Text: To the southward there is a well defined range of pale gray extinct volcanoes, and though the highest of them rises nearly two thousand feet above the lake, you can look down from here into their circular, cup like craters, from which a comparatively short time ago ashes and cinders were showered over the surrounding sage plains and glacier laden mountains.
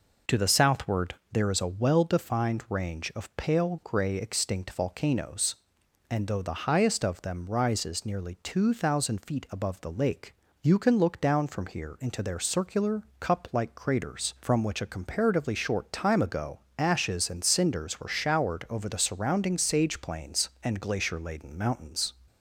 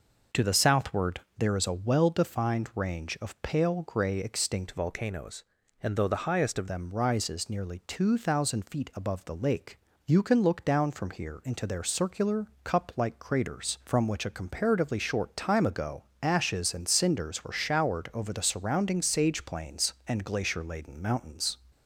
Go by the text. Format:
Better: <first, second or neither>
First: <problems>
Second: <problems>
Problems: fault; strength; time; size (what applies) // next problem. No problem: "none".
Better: first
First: pauses between "southward" and "there"; slight; at 1.1 s; 0.18 s long // pauses between "ago" and "ashes"; slight; at 16.5 s; 0.18 s long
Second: pauses between "southward" and "there"; slight; at 1.1 s; 0.18 s long // changes voice from "volcanoes" to "of"; from 4.7 to 6.6 s; 1.9 s long // pauses between "ago" and "ashes"; slight; at 16.0 s; 0.18 s long